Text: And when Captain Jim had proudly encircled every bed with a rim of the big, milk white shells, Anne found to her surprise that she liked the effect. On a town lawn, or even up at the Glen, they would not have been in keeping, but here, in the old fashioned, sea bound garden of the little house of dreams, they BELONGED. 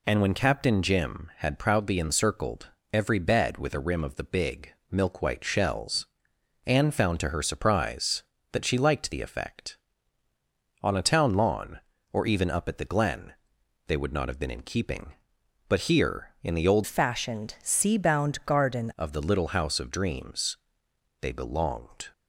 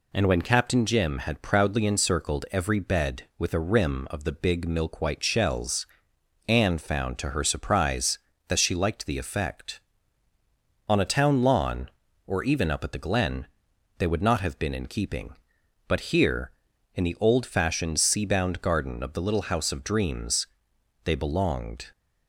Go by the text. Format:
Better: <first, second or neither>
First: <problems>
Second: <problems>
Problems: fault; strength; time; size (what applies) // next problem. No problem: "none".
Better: second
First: pauses between "encircled" and "every"; slight; at 2.6 s; 0.22 s long // changes voice from "fashioned" to "garden"; from 16.8 to 18.9 s; 2.1 s long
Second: none